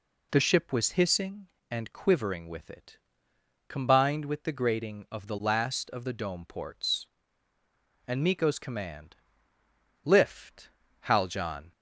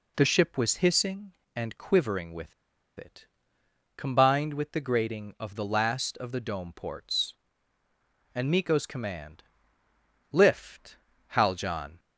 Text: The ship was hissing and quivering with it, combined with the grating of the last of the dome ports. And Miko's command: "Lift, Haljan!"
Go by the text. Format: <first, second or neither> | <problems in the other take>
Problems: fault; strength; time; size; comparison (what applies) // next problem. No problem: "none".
first | pauses between "with" and "it"; at 2.5 s; 0.45 s long